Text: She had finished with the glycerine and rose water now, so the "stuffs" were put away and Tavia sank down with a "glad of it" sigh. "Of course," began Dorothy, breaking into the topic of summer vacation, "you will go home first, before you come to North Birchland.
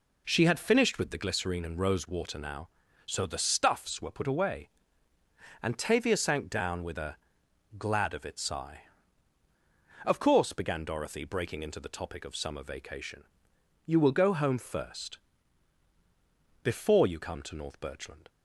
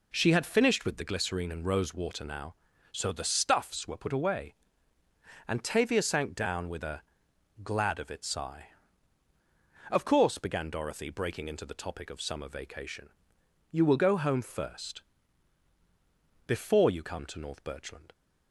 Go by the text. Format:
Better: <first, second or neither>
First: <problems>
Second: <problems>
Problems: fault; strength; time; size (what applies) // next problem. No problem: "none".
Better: neither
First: pauses between "a" and "glad"; noticeable; at 7.1 s; 0.62 s long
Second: pauses between "a" and "glad"; noticeable; at 7.0 s; 0.62 s long